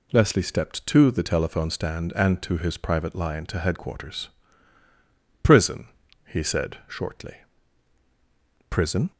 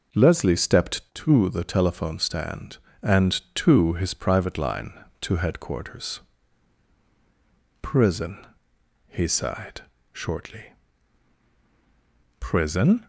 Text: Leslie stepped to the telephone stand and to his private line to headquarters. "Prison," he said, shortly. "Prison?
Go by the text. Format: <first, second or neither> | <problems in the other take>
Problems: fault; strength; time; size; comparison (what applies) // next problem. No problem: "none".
first | says "sighed" for "said"; at 9.2 s